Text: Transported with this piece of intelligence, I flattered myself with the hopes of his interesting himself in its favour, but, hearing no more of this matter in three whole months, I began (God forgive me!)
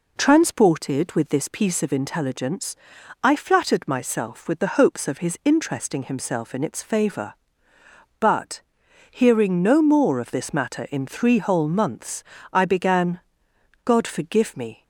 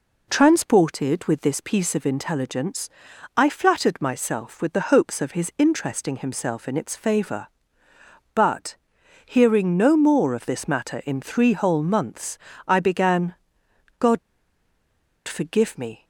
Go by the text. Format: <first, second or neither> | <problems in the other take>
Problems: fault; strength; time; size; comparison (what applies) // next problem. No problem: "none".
first | pauses between "God" and "forgive"; at 14.1 s; 1.0 s long